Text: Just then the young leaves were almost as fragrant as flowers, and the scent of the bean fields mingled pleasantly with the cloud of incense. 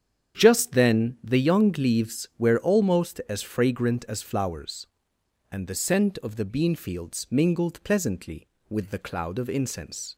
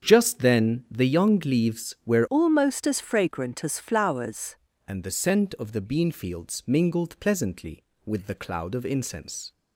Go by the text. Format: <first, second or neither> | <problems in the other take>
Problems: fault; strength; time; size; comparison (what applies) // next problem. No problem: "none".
first | starts louder than the rest; strong; until 1.1 s; 7.5 dB; strong in the first // changes voice from "almost" to "flowers"; from 2.2 to 4.5 s; 2.3 s long